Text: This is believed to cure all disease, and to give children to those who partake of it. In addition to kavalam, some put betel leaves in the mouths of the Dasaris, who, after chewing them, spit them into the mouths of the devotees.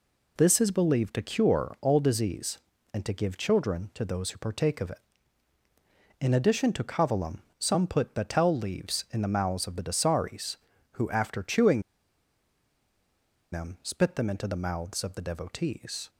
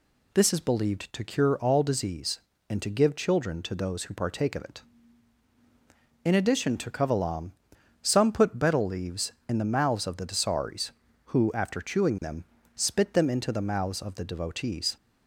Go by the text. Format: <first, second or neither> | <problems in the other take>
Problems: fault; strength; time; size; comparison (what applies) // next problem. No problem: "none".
second | pauses between "chewing" and "them"; strong; at 11.8 s; 1.7 s long